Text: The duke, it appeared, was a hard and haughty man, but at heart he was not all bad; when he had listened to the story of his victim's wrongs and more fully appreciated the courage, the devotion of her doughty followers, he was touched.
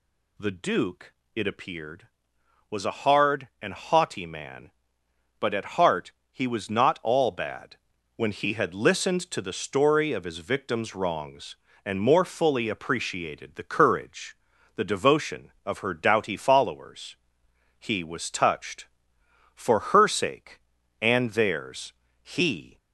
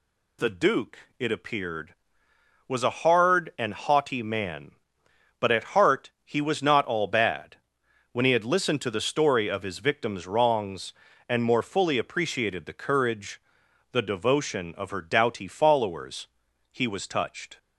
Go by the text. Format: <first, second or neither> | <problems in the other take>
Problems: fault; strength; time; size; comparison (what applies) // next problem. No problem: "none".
second | pauses between "heart" and "he"; slight; at 6.1 s; 0.20 s long // goes on to say "For her sake and theirs he"; strong; from 19.5 s on; 3.2 s long